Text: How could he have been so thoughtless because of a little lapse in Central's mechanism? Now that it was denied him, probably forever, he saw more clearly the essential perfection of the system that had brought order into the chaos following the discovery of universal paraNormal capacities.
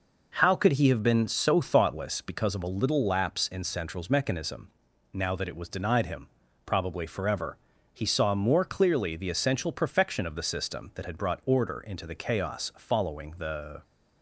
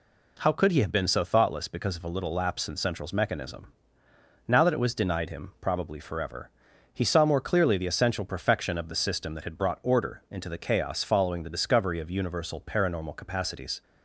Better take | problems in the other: second | stops before "discovery of universal paraNormal capacities"; at 13.8 s

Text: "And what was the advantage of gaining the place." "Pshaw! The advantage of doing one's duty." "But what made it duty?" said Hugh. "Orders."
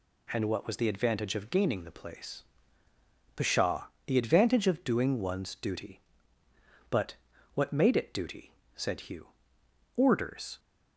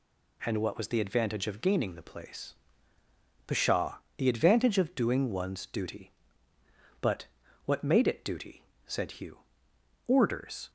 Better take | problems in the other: neither | pauses between "But" and "what"; the same in both

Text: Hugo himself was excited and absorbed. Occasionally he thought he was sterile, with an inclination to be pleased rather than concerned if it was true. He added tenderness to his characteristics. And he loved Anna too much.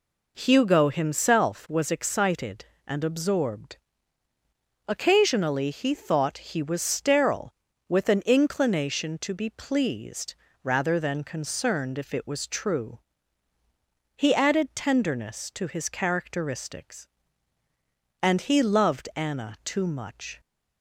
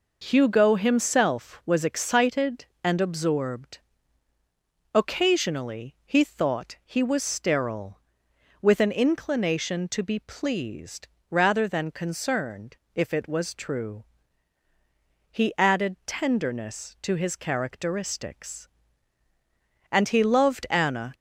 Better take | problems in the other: first | pauses between "pleased" and "rather"; slight; at 11.0 s; 0.24 s long; slight in the first // pauses between "concerned" and "if"; slight; at 12.7 s; 0.18 s long // stops before "too much"; at 21.1 s

